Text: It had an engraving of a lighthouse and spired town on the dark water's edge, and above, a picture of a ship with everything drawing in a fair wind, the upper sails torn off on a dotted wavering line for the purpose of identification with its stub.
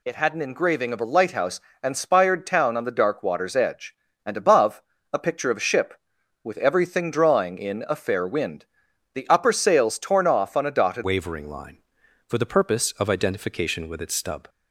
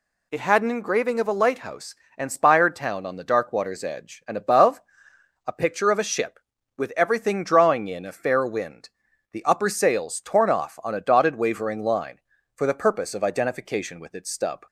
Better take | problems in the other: second | changes voice at "wavering"; from 11.0 s on; 3.4 s long

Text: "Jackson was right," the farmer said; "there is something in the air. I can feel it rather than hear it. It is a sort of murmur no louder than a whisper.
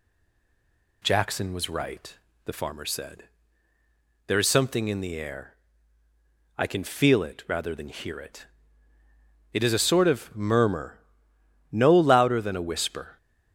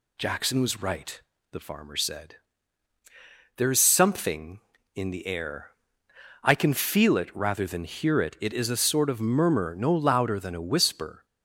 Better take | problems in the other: second | stays silent before the first word; until 1.0 s; 1.0 s long // pauses between "murmur" and "no"; noticeable; at 10.9 s; 0.74 s long

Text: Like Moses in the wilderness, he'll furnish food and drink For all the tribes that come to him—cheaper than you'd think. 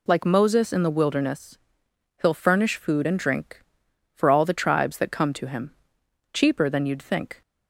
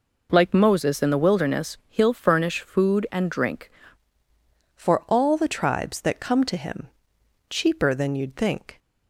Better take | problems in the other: first | changes voice at "For"; from 4.7 s on; 4.0 s long

